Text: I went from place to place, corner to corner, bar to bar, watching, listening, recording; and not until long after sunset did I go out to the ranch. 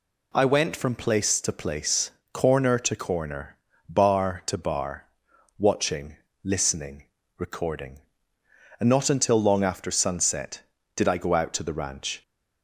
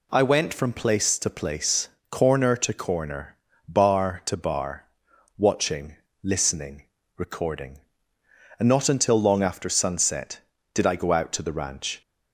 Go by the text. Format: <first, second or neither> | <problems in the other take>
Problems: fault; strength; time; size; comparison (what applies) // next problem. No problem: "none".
neither | none